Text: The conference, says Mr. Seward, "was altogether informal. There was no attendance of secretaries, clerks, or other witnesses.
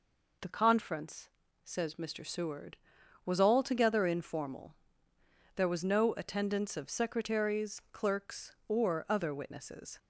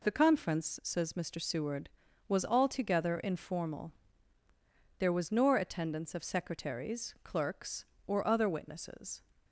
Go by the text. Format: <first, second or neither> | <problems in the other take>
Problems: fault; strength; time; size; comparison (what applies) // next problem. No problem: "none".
first | says "nor" for "no"; at 5.3 s